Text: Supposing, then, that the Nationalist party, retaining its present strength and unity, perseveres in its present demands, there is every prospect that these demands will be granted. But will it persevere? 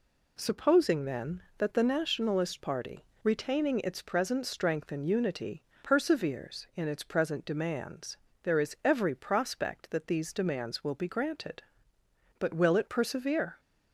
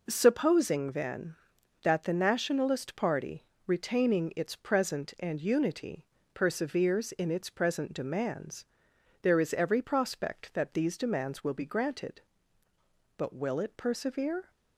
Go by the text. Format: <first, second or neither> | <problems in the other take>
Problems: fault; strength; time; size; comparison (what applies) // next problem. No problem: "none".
first | skips "strength"; at 5.1 s